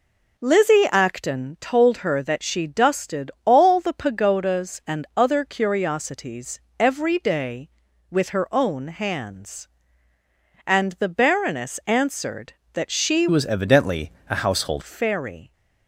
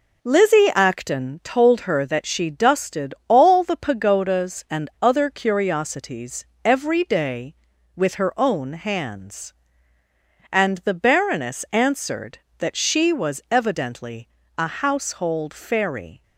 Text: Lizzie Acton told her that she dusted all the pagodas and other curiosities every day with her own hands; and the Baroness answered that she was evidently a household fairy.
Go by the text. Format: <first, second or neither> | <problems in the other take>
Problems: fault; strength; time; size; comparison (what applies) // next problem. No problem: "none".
second | pauses between "curiosities" and "every"; slight; at 6.5 s; 0.20 s long; slight in the second // changes voice from "was" to "household"; from 13.3 to 14.8 s; 1.5 s long // pauses between "evidently" and "a"; slight; at 14.1 s; 0.18 s long; slight in the second